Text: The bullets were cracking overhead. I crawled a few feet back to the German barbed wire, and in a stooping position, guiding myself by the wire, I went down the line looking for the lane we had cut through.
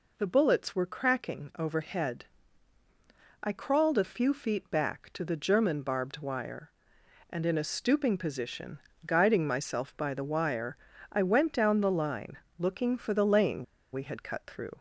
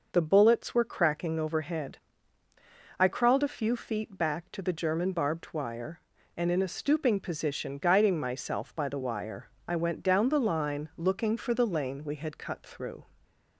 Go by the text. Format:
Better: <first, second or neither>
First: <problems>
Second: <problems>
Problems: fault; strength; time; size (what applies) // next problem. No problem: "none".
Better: second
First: pauses between "line" and "looking"; slight; at 12.3 s; 0.22 s long // pauses between "lane" and "we"; slight; at 13.6 s; 0.28 s long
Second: none